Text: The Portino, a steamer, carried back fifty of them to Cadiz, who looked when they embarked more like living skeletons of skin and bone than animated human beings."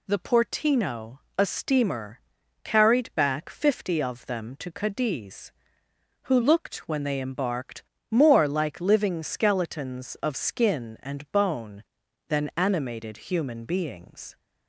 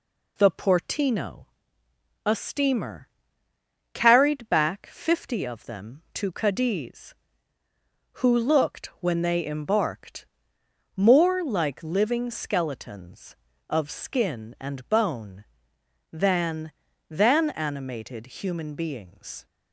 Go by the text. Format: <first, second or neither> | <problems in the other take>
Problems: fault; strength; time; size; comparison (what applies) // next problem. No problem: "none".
first | pauses between "embarked" and "more"; noticeable; at 10.2 s; 0.70 s long; slight in the first // says "than" twice; at 17.1 s